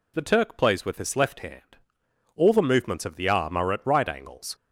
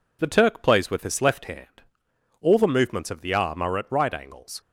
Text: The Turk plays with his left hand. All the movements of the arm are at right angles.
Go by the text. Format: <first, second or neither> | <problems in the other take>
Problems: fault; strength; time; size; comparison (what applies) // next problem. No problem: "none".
first | gets quieter; slight; throughout; 2 dB